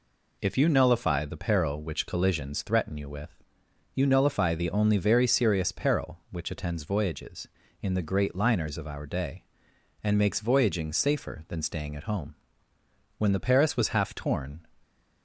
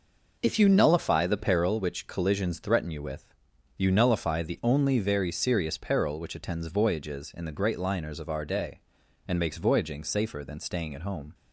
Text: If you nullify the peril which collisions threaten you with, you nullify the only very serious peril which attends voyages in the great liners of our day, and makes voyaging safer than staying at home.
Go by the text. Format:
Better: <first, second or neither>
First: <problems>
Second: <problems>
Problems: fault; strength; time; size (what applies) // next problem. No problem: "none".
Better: second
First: goes on to say "When the Paris was half torn"; from 13.1 s on; 1.4 s long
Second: none